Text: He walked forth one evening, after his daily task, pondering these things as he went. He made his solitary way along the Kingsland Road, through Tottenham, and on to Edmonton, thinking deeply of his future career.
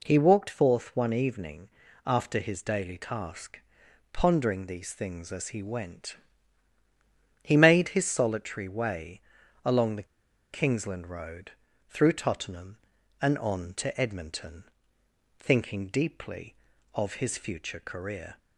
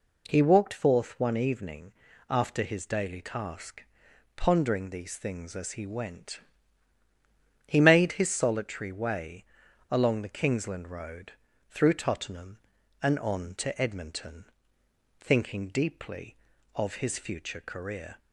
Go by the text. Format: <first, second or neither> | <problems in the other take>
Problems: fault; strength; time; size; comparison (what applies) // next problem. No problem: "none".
second | pauses between "way" and "along"; at 9.2 s; 0.44 s long; noticeable in the second // pauses between "the" and "Kingsland"; noticeable; at 10.0 s; 0.46 s long